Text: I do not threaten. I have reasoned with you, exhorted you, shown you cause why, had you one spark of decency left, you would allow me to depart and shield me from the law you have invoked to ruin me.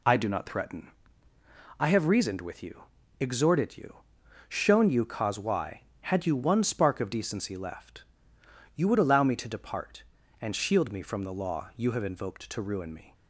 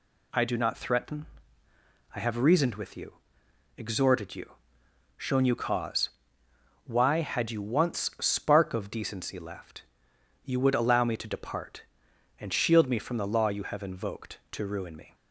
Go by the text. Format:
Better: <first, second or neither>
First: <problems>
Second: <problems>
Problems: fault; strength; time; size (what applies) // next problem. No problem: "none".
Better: first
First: none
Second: pauses between "cause" and "why"; noticeable; at 6.0 s; 0.78 s long // says "once" for "one"; at 7.6 s